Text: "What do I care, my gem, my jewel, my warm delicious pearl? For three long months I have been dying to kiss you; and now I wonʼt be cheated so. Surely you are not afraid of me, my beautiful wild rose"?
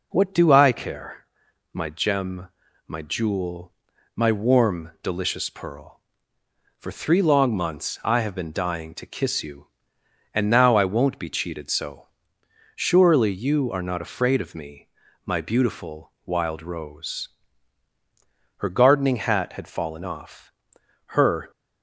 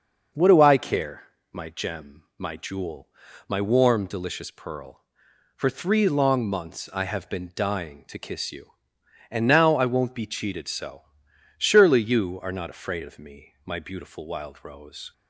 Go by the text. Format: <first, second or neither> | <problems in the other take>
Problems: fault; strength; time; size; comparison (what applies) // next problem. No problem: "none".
second | goes on to say "Her gardening hat had fallen off her"; strong; from 18.5 s on; 2.9 s long